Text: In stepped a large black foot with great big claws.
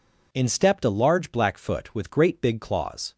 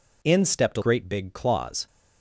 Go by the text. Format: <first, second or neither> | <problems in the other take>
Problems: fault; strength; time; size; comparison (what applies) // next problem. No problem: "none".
first | skips "large black foot with"; at 0.8 s